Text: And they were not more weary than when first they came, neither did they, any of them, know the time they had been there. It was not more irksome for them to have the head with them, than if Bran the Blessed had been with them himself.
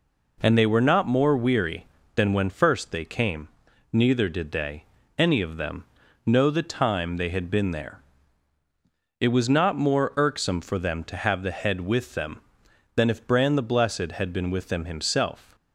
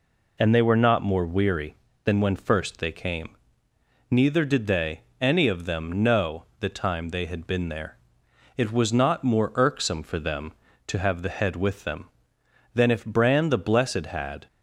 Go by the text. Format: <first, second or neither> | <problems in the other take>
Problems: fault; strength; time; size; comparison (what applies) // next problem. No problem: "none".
first | pauses between "know" and "the"; slight; at 6.4 s; 0.16 s long // stops before "been with them himself"; at 14.4 s